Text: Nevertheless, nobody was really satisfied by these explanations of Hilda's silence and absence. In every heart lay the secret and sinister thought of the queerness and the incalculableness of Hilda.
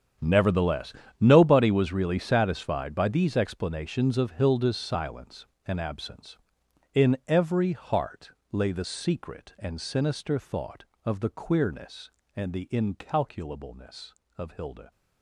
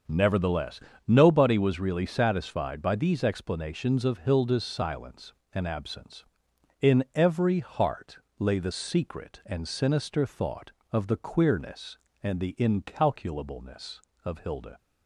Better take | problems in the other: second | gets quieter; strong; throughout; 16 dB // starts louder than the rest; strong; until 1.4 s; 8.5 dB; also in the second // pauses between "heart" and "lay"; slight; at 8.3 s; 0.22 s long; slight in the second

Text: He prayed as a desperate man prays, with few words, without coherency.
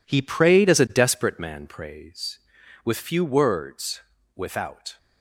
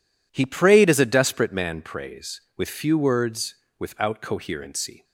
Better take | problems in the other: second | stops before "coherency"; at 4.9 s

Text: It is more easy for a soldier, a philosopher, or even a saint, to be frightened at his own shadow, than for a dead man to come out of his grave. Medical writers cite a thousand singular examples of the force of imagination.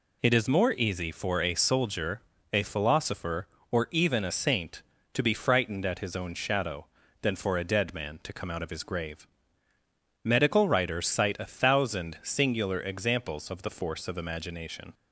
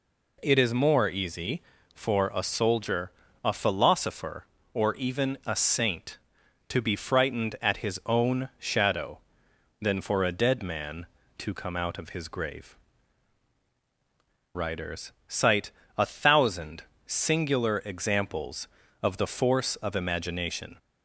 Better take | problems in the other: first | skips "Medical"; at 13.6 s // pauses between "writers" and "cite"; slight; at 15.1 s; 0.16 s long // pauses between "cite" and "a"; slight; at 15.7 s; 0.26 s long // pauses between "thousand" and "singular"; slight; at 16.8 s; 0.22 s long

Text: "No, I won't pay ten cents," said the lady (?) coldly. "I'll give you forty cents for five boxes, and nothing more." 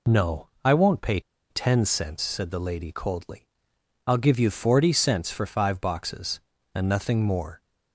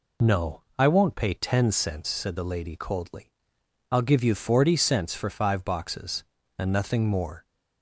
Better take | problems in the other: second | pauses between "pay" and "ten"; slight; at 1.1 s; 0.30 s long

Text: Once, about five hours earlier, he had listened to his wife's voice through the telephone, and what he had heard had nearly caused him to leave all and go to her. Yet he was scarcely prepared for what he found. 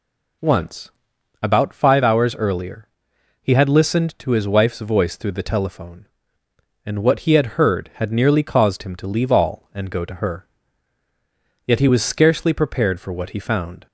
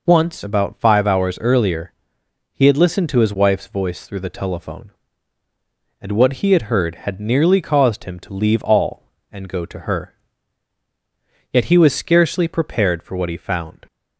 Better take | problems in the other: neither | none

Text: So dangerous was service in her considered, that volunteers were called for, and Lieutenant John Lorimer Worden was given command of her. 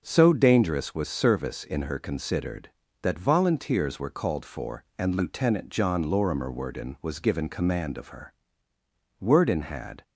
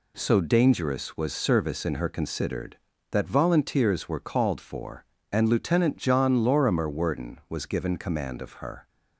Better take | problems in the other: second | starts louder than the rest; until 1.0 s; 6 dB // goes on to say "Worden had"; noticeable; from 9.2 s on; 0.82 s long

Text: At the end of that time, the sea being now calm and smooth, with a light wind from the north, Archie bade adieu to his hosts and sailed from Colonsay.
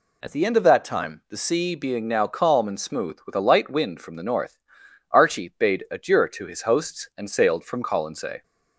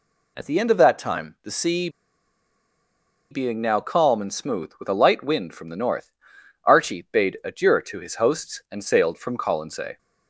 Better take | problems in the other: first | pauses between "sea" and "being"; strong; at 1.8 s; 1.4 s long

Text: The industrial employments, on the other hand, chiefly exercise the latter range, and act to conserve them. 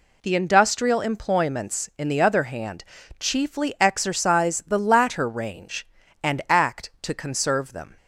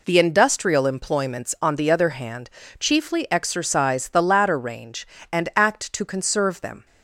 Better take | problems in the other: second | says "in" for "on"; at 1.9 s

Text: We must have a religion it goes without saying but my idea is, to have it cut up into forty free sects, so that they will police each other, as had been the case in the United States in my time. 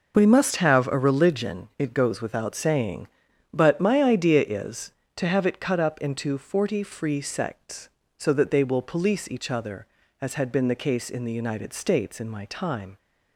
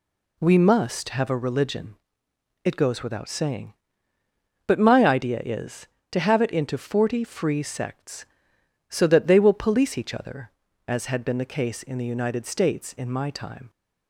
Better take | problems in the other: first | pauses between "religion" and "it"; noticeable; at 1.9 s; 0.68 s long // skips "cut up"; at 6.5 s

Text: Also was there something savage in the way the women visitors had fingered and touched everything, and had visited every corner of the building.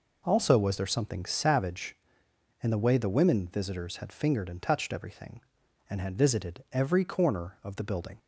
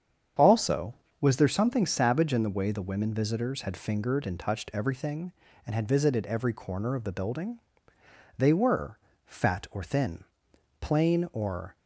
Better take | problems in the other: first | starts louder than the rest; strong; until 1.6 s; 8 dB // goes on to say "They were fat or thin plain or"; strong; from 8.3 s on; 3.4 s long

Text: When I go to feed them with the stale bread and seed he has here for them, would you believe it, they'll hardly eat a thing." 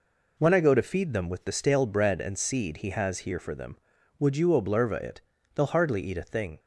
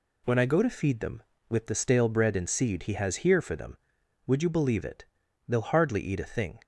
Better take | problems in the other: second | says "oblerva" for "believe"; at 4.4 s

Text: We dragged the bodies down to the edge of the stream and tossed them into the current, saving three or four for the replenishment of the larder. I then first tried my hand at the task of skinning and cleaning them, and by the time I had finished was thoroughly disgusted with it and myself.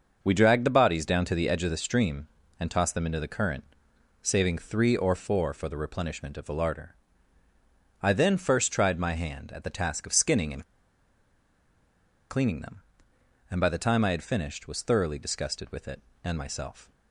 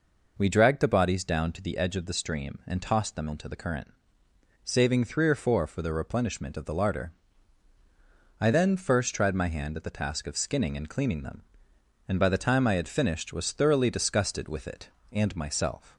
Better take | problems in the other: second | pauses between "and" and "cleaning"; strong; at 10.6 s; 1.6 s long

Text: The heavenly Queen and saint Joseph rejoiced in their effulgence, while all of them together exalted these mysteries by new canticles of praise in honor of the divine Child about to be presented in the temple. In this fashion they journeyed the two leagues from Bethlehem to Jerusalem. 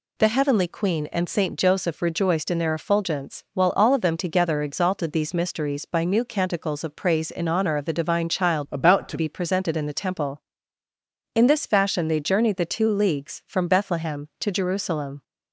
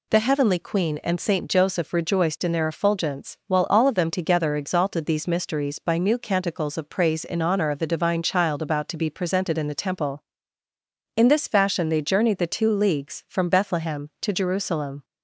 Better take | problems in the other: second | changes voice from "about" to "to"; from 8.6 to 9.1 s; 0.5 s long

